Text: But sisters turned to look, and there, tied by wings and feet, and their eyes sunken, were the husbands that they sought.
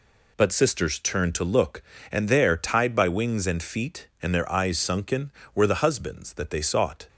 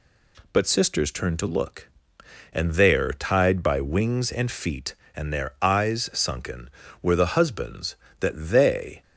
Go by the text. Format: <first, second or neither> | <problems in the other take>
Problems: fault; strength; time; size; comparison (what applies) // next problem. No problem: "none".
first | stops before "sought"; at 9.0 s